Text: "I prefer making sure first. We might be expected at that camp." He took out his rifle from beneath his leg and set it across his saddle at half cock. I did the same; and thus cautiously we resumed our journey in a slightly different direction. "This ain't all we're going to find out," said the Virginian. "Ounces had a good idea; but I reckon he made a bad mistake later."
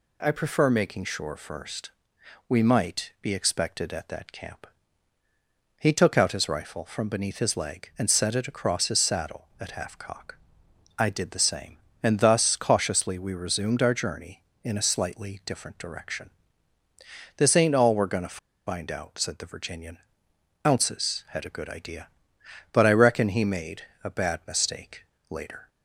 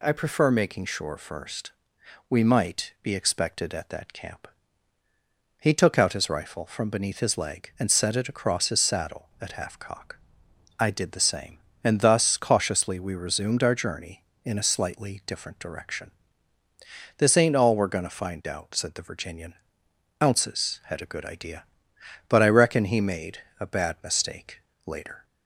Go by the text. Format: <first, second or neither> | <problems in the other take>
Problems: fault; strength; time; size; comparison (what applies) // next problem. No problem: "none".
second | pauses between "to" and "find"; slight; at 18.3 s; 0.27 s long // pauses between "made" and "a"; slight; at 23.8 s; 0.20 s long; slight in the second // pauses between "mistake" and "later"; slight; at 25.0 s; 0.24 s long; slight in the second